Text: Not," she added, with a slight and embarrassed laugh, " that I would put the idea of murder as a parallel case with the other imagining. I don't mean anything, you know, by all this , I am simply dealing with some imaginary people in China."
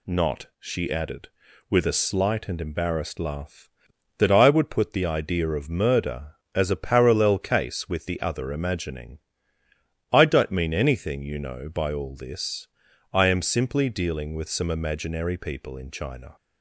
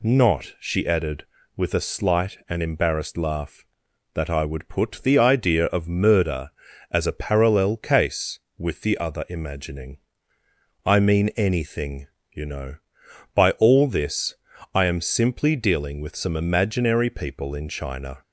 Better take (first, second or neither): first